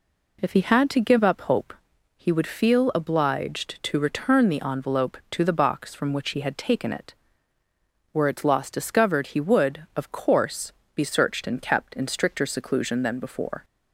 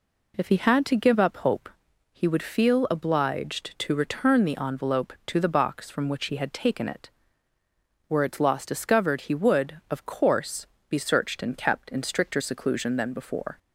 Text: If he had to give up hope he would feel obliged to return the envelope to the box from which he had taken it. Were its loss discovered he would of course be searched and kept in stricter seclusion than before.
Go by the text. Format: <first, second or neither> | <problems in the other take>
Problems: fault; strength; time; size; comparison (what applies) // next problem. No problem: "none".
neither | pauses between "hope" and "he"; the same in both // pauses between "course" and "be"; slight; the same in both